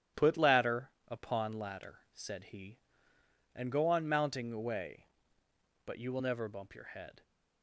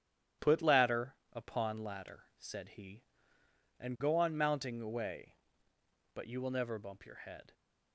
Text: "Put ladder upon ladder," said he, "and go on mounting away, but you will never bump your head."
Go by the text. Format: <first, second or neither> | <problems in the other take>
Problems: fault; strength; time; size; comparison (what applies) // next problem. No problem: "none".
neither | starts louder than the rest; strong; the same in both // pauses between "ladder" and "upon"; slight; the same in both